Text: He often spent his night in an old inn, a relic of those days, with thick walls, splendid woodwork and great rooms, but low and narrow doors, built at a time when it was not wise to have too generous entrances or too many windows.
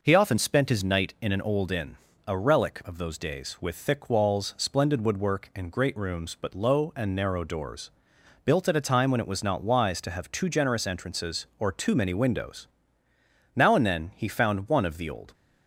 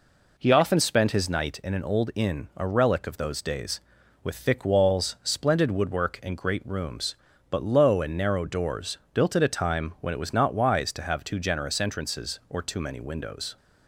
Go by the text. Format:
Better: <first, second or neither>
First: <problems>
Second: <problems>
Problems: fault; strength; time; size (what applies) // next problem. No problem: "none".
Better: second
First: goes on to say "Now and then he found one of the old"; strong; from 13.5 s on; 1.7 s long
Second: none